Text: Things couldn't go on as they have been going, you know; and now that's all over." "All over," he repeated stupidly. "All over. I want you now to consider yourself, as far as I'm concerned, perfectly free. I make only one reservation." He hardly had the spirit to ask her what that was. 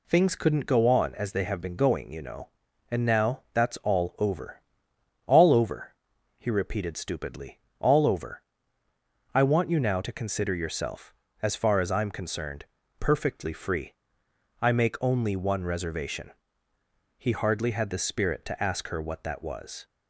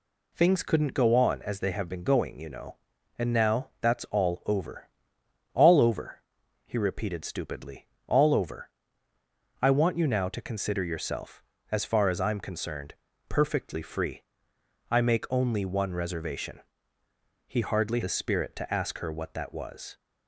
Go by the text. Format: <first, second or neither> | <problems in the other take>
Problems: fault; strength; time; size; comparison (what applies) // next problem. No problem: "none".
first | skips "had"; at 18.0 s